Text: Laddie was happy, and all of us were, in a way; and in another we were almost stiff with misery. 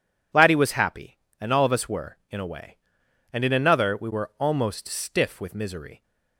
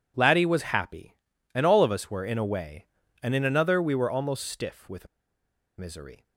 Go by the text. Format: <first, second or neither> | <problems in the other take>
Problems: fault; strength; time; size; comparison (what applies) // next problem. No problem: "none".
first | pauses between "with" and "misery"; noticeable; at 5.0 s; 0.72 s long